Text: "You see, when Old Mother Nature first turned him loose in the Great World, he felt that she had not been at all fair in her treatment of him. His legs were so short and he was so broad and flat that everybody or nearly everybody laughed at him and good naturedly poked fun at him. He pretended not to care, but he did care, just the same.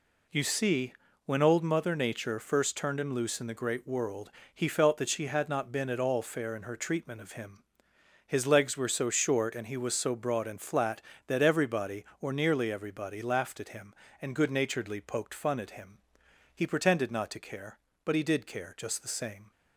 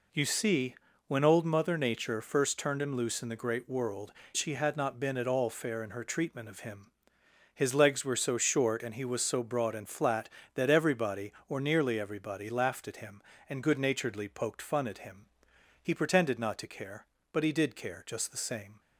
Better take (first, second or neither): first